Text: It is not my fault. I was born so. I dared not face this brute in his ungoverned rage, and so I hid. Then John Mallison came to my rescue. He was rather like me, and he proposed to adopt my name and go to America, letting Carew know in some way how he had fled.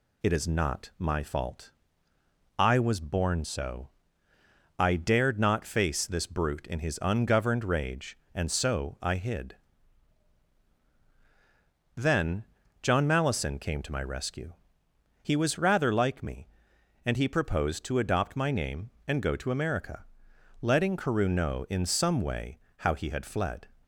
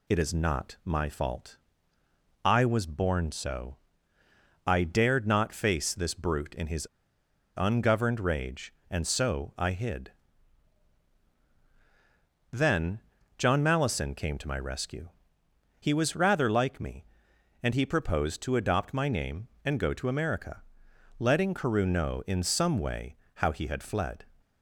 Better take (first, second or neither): first